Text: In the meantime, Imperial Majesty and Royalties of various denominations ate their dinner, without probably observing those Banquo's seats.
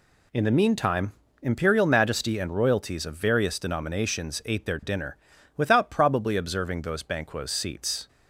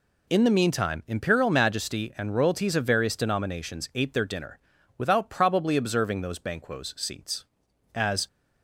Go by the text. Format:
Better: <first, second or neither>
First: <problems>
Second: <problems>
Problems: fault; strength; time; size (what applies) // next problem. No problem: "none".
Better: first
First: none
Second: goes on to say "As"; slight; from 7.9 s on; 0.32 s long